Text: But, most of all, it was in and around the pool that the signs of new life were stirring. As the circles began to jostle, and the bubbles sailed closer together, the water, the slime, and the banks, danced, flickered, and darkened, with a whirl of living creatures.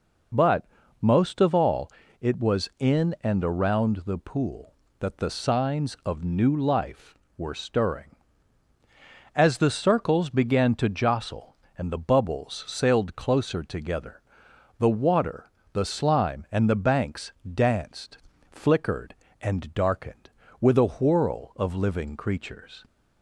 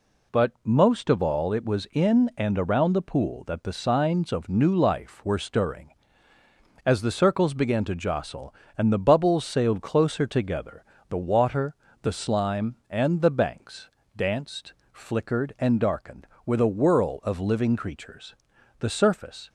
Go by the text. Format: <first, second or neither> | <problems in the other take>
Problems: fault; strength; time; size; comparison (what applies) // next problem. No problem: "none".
first | goes on to say "The surface"; noticeable; from 18.7 s on; 0.70 s long